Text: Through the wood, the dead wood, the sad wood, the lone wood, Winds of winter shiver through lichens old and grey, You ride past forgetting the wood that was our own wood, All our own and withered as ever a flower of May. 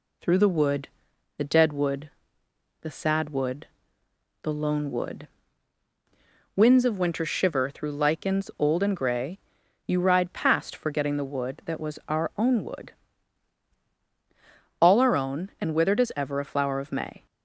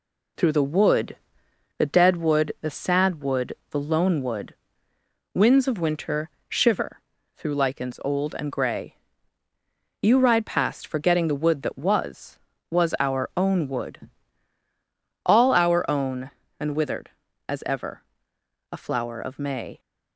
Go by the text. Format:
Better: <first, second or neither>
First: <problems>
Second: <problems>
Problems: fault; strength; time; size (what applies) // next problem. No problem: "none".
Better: first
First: none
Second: pauses between "winter" and "shiver"; slight; at 6.2 s; 0.18 s long // pauses between "shiver" and "through"; slight; at 7.0 s; 0.36 s long // says "was" twice; at 12.6 s // pauses between "ever" and "a"; noticeable; at 18.0 s; 0.72 s long